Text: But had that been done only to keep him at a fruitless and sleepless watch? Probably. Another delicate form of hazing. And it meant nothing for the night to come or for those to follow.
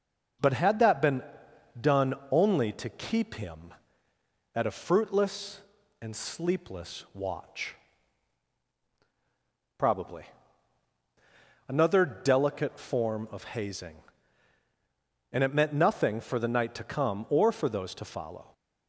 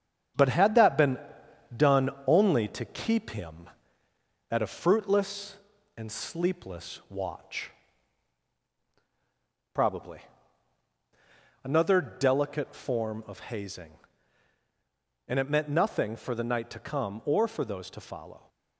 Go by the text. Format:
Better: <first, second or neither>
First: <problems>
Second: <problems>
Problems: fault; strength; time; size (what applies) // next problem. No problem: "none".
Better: first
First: starts louder than the rest; until 1.9 s; 6.5 dB // pauses between "been" and "done"; noticeable; at 1.2 s; 0.56 s long // pauses between "done" and "only"; slight; at 2.1 s; 0.16 s long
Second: gets quieter; noticeable; throughout; 5.5 dB // starts louder than the rest; strong; until 1.9 s; 8.5 dB // pauses between "been" and "done"; noticeable; at 1.1 s; 0.56 s long // pauses between "done" and "only"; slight; at 2.1 s; 0.16 s long